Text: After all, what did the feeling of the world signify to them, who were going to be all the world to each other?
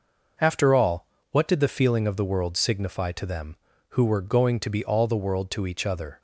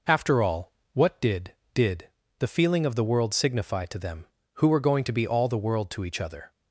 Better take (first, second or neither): first